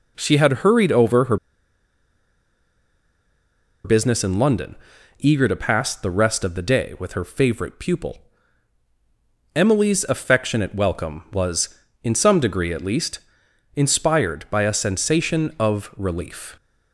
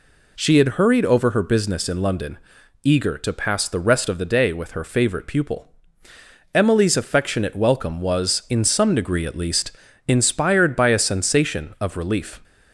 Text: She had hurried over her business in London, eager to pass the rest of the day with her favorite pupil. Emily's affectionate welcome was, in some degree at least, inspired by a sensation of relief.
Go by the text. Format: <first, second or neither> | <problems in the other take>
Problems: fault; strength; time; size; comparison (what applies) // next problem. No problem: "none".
second | pauses between "her" and "business"; strong; at 1.3 s; 2.4 s long